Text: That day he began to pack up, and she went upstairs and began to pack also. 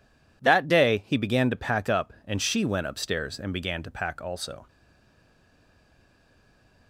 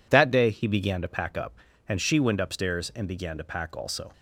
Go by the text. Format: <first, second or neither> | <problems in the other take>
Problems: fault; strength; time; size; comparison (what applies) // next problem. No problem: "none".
second | stays silent after the last word; from 4.6 s on; 2.2 s long